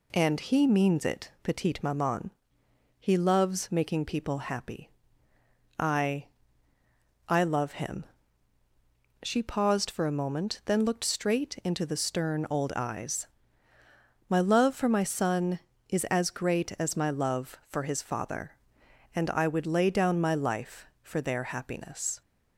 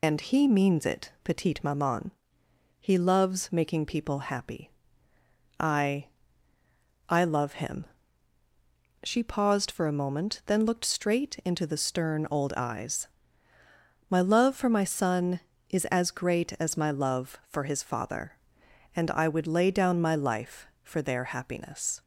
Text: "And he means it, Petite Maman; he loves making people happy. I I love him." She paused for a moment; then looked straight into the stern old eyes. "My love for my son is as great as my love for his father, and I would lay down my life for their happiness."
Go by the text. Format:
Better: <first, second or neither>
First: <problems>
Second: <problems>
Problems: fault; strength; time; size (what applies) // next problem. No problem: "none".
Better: first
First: pauses between "I" and "I"; at 6.2 s; 1.0 s long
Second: loses the start of "And"; at 0.0 s; 125 ms // pauses between "I" and "I"; at 6.0 s; 1.0 s long